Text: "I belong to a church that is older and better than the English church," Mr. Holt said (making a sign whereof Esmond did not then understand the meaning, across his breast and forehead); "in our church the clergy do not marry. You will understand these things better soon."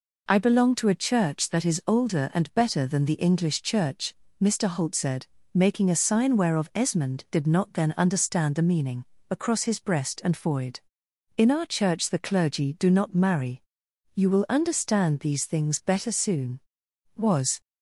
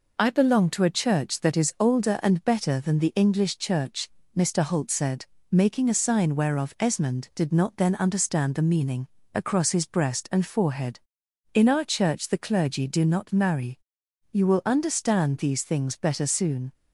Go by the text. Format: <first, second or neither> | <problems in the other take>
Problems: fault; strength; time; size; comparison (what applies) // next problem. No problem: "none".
second | goes on to say "Was"; slight; from 17.1 s on; 0.44 s long